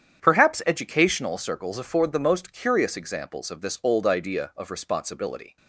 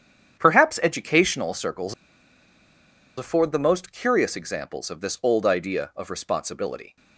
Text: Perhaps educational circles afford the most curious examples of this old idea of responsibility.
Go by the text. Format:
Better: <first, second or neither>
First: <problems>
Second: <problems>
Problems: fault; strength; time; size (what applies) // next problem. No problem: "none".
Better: first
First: starts louder than the rest; strong; until 1.2 s; 9 dB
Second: starts louder than the rest; strong; until 1.4 s; 9 dB // pauses between "circles" and "afford"; at 1.9 s; 1.2 s long